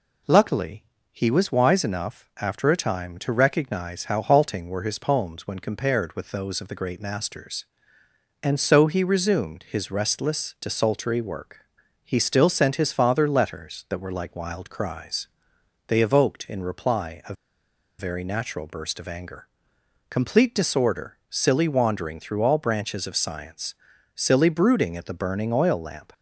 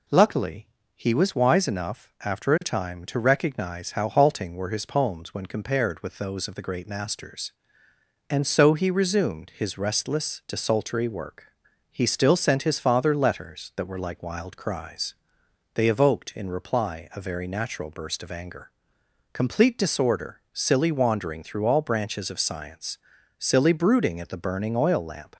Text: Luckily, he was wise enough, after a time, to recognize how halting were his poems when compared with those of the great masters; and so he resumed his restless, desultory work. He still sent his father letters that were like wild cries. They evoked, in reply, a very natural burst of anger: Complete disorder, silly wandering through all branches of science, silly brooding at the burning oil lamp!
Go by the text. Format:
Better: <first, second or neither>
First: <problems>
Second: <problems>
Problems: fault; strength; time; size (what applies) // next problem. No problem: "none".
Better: second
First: pauses between "a" and "very"; noticeable; at 17.3 s; 0.65 s long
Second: none